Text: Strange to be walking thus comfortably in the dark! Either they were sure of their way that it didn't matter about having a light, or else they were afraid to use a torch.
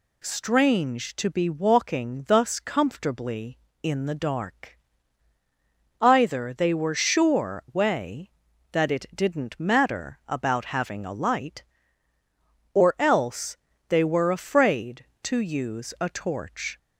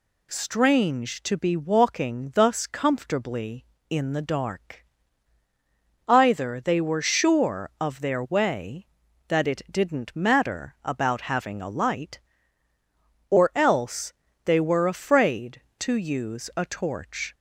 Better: second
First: skips "of their"; at 7.6 s // pauses between "else" and "they"; slight; at 13.5 s; 0.32 s long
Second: pauses between "else" and "they"; slight; at 14.1 s; 0.32 s long

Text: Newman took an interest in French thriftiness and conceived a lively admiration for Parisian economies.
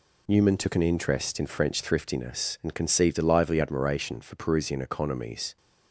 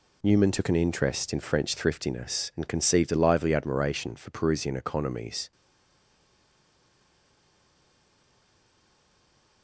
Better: first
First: none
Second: stays silent after the last word; strong; from 5.5 s on; 4.1 s long

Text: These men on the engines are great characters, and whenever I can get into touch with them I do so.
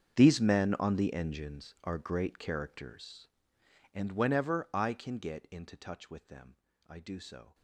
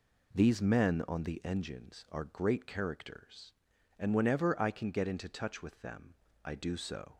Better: second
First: gets quieter; strong; throughout; 19.5 dB // pauses between "them" and "I"; slight; at 6.5 s; 0.32 s long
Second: pauses between "them" and "I"; slight; at 6.1 s; 0.28 s long

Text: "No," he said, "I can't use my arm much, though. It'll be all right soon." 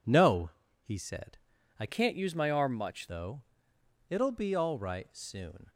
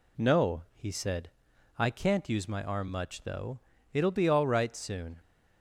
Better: second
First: changes voice from "can't" to "much"; from 1.8 to 3.0 s; 1.2 s long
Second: none

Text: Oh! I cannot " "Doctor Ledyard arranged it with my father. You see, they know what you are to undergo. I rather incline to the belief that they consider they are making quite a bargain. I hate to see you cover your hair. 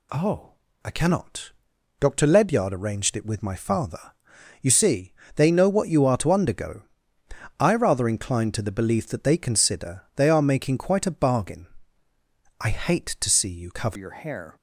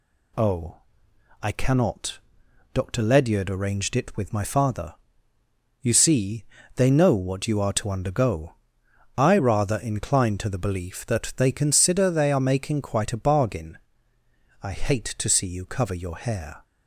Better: second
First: changes voice at "your"; from 13.9 s on; 0.6 s long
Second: none

